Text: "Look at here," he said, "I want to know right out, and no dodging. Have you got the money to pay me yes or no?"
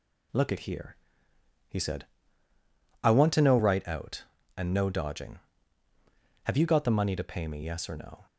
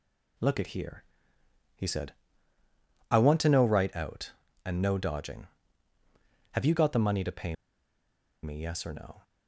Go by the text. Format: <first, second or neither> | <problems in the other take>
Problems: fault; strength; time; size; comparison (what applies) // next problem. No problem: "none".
first | pauses between "pay" and "me"; noticeable; at 7.5 s; 0.88 s long